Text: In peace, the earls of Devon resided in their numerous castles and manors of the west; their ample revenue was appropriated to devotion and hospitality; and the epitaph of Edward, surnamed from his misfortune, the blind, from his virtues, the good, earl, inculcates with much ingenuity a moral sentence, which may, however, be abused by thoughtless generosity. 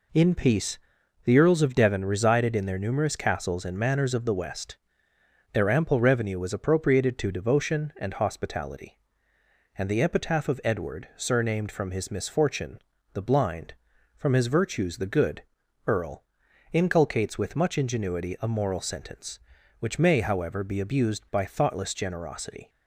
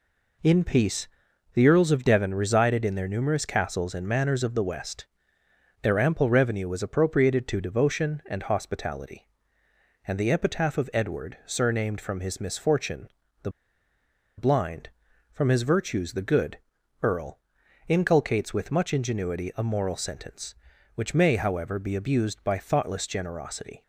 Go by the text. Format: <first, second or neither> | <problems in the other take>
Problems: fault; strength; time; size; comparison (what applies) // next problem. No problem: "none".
first | pauses between "the" and "blind"; noticeable; at 13.4 s; 0.87 s long